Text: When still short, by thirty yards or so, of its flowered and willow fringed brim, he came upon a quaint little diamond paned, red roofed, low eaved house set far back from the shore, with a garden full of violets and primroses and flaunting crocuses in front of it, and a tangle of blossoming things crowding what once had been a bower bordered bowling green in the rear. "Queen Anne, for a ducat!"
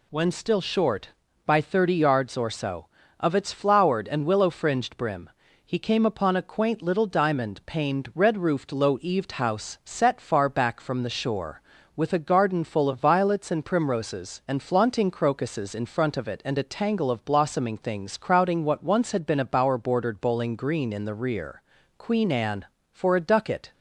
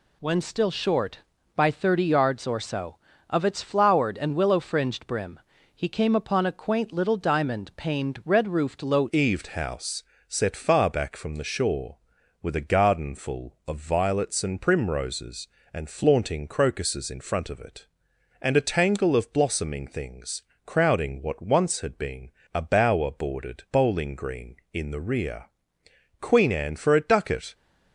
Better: first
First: none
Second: changes voice at "eaved"; from 9.0 s on; 18.5 s long // pauses between "house" and "set"; slight; at 10.0 s; 0.26 s long // pauses between "things" and "crowding"; slight; at 20.4 s; 0.24 s long // pauses between "been" and "a"; slight; at 22.3 s; 0.24 s long

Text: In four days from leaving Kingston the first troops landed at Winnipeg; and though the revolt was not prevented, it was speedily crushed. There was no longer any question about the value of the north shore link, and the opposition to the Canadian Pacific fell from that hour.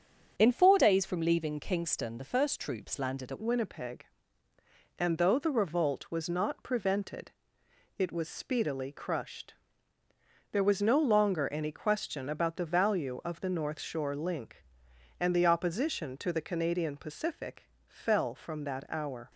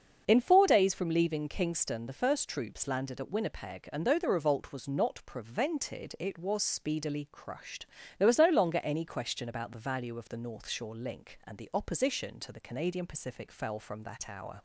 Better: second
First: starts louder than the rest; until 1.3 s; 7 dB // changes voice at "Winnipeg"; from 3.3 s on; 16.0 s long // pauses between "Pacific" and "fell"; slight; at 17.6 s; 0.18 s long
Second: starts louder than the rest; until 1.2 s; 6.5 dB

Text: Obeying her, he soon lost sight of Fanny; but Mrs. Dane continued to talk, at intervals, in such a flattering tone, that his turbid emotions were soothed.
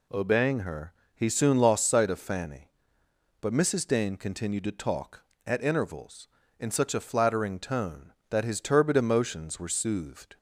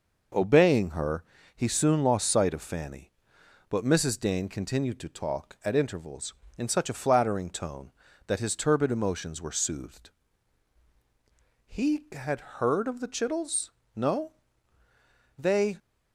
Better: first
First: none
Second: goes on to say "He had heard of the Chittles No They"; strong; from 11.6 s on; 4.1 s long

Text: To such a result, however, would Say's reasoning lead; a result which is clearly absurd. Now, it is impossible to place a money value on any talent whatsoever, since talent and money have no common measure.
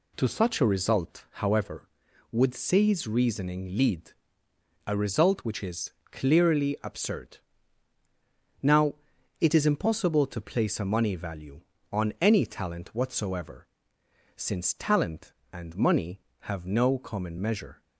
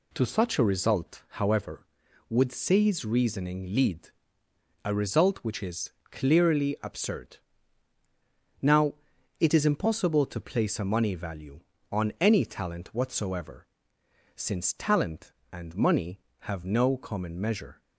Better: neither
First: pauses between "is" and "clearly"; slight; at 5.9 s; 0.20 s long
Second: pauses between "is" and "clearly"; slight; at 5.9 s; 0.20 s long

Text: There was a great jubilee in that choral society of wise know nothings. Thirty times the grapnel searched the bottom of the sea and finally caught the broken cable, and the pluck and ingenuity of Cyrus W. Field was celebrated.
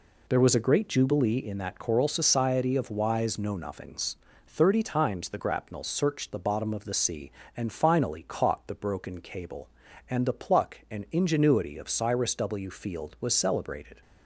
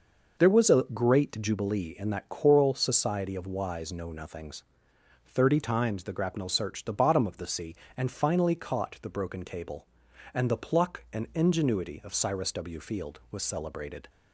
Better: neither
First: none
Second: none

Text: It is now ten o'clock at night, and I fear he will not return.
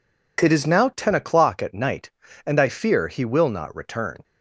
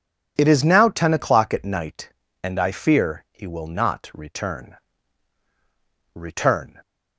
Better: first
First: none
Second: says "return" twice; at 6.1 s

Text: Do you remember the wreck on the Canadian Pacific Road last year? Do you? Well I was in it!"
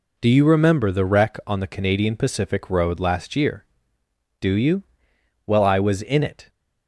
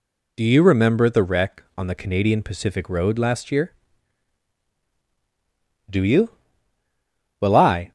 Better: first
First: none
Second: stops before "was in it"; at 7.8 s

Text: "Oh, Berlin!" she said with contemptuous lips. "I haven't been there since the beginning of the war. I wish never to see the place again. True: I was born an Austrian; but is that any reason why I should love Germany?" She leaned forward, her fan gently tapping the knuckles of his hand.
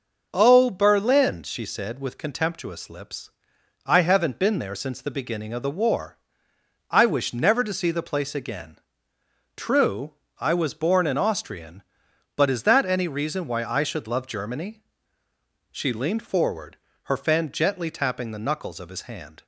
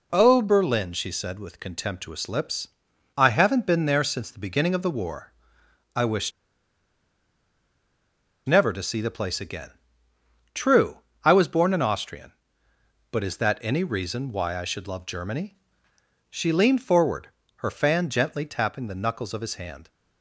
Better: first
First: none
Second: pauses between "wish" and "never"; strong; at 6.3 s; 2.1 s long

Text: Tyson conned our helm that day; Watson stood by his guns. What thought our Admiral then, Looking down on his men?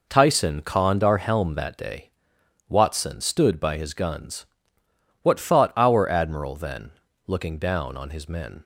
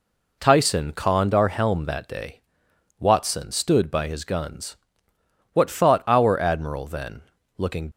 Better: first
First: none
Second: stops before "down on his men"; at 7.9 s

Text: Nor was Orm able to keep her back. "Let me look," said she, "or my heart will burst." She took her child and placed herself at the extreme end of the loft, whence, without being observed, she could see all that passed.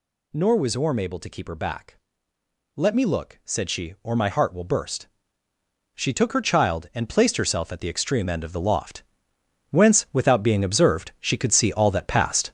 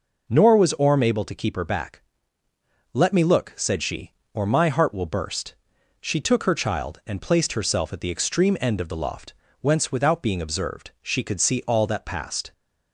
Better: second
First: gets louder; strong; throughout; 7 dB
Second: none

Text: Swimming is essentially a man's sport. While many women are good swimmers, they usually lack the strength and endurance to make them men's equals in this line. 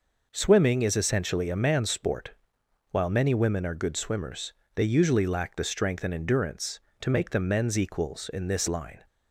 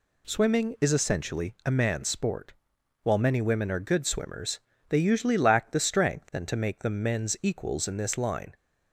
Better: first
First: none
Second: skips "endurance"; at 6.4 s

